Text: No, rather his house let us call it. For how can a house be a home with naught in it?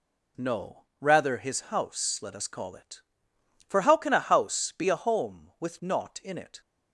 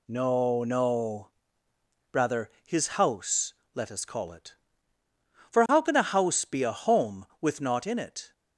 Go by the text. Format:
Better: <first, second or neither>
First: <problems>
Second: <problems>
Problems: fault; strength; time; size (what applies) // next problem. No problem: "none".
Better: first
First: none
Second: says "No" twice; at 0.6 s // pauses between "rather" and "his"; slight; at 2.4 s; 0.16 s long // pauses between "house" and "let"; slight; at 3.5 s; 0.20 s long